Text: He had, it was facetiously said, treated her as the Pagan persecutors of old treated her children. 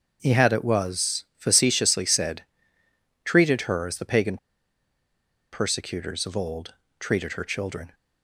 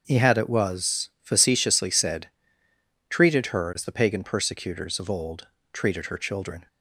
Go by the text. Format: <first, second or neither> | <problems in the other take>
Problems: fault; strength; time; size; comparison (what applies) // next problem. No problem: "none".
second | starts louder than the rest; noticeable; until 1.2 s; 6 dB; also in the second // pauses between "Pagan" and "persecutors"; at 4.3 s; 1.1 s long // pauses between "old" and "treated"; slight; at 6.7 s; 0.26 s long; slight in the second